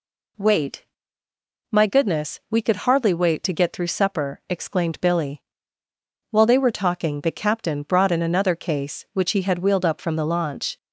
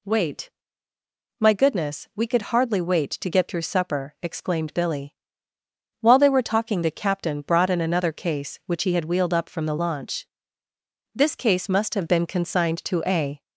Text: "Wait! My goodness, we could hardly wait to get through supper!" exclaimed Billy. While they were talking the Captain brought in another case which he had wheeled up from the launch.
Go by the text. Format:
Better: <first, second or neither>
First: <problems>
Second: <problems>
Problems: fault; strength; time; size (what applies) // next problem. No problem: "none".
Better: first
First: none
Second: goes on to say "This case must have been consigned to a"; strong; from 11.1 s on; 2.2 s long